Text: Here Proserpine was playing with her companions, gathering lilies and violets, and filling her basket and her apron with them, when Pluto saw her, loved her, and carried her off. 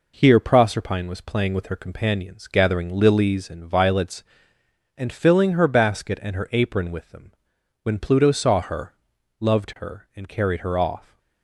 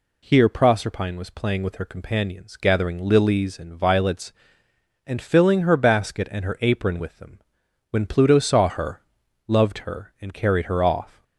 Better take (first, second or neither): second